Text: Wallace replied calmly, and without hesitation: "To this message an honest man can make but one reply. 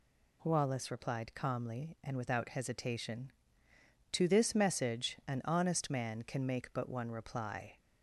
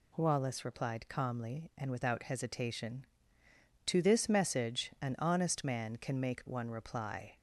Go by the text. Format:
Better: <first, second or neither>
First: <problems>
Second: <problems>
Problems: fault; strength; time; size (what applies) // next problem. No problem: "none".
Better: first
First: none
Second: skips "but"; at 6.4 s